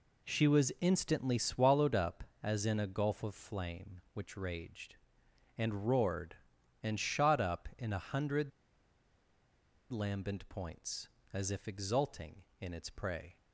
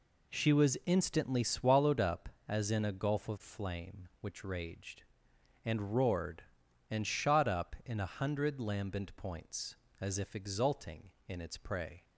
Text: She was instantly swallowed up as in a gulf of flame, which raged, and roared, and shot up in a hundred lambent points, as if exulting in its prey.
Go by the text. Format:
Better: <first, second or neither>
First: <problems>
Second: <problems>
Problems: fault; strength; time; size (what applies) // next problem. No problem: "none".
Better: second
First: pauses between "hundred" and "lambent"; strong; at 8.5 s; 1.3 s long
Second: none